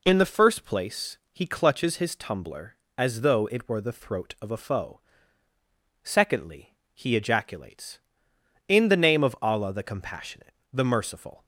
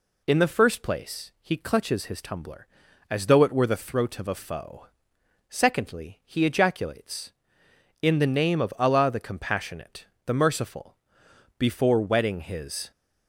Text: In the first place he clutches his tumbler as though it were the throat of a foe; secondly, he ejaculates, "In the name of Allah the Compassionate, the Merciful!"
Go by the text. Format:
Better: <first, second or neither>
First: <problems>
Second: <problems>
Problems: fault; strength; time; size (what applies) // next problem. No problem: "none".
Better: first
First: none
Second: goes on to say "before wetting his"; from 11.5 s on; 1.3 s long